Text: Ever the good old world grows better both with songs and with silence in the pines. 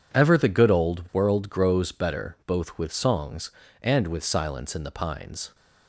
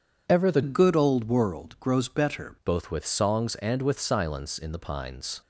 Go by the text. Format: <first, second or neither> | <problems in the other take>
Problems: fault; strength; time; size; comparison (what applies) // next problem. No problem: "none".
first | changes voice from "good" to "better"; from 0.6 to 2.5 s; 1.9 s long